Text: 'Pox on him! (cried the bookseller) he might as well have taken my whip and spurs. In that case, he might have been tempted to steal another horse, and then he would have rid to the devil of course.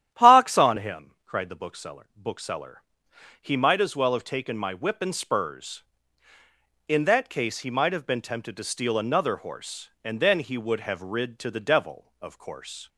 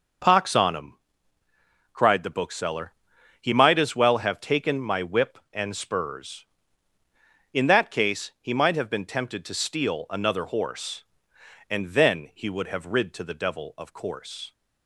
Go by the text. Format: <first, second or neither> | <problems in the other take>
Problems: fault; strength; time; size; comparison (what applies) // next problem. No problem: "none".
second | starts louder than the rest; strong; until 1.1 s; 10.5 dB; also in the second // says "bookseller" twice; at 2.1 s